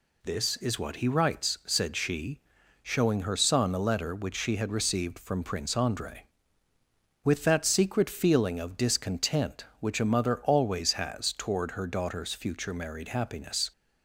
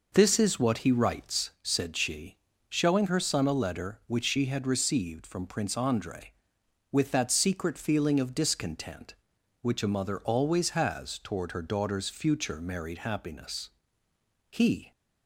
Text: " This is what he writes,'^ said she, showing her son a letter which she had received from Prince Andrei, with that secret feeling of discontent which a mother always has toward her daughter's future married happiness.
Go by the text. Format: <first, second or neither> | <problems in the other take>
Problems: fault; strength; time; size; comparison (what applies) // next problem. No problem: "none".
first | goes on to say "He"; slight; from 14.5 s on; 0.40 s long